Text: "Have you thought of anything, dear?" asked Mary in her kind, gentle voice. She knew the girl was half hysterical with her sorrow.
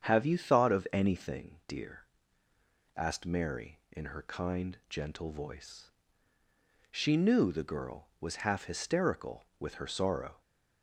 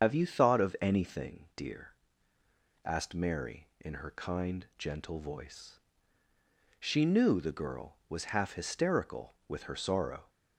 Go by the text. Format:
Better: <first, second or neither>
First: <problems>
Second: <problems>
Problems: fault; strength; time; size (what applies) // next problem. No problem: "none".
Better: first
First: starts louder than the rest; strong; until 1.1 s; 7.5 dB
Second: loses the start of "Have"; at 0.0 s; 110 ms // starts louder than the rest; until 1.0 s; 7 dB